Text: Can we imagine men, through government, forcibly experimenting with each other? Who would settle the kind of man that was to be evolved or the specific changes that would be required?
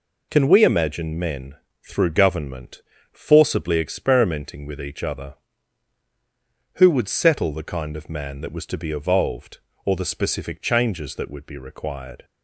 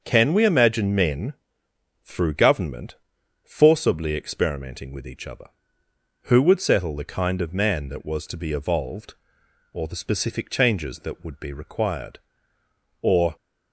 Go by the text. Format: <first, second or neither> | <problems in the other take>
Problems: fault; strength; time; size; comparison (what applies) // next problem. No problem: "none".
first | starts louder than the rest; until 1.0 s; 6.5 dB // goes on to say "Or"; slight; from 13.0 s on; 0.34 s long